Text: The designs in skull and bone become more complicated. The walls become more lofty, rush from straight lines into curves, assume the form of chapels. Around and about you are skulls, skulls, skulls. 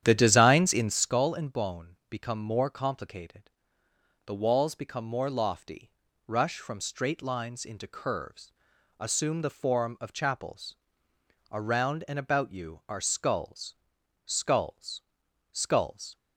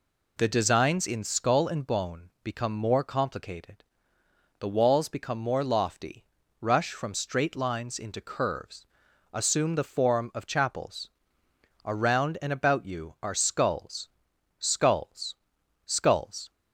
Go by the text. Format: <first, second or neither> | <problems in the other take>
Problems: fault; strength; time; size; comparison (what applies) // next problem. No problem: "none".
second | starts louder than the rest; strong; until 1.2 s; 10 dB